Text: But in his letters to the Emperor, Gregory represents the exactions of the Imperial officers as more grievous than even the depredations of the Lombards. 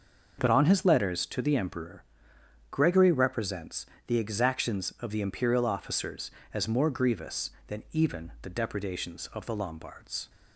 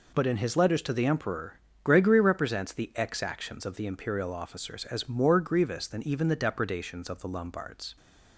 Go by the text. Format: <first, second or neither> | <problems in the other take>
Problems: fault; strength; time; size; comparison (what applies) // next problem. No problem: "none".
second | starts louder than the rest; noticeable; until 1.4 s; 6 dB // says "on" for "in"; at 0.4 s // pauses between "represents" and "the"; slight; at 3.8 s; 0.22 s long